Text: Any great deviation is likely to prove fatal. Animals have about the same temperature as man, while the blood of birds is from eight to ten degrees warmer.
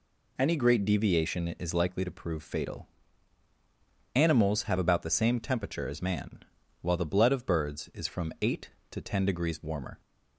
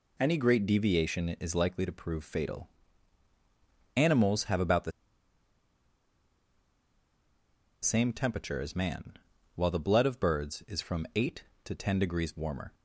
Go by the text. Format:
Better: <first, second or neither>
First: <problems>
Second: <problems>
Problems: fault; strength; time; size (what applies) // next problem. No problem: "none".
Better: first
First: none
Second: pauses between "the" and "same"; strong; at 4.9 s; 2.9 s long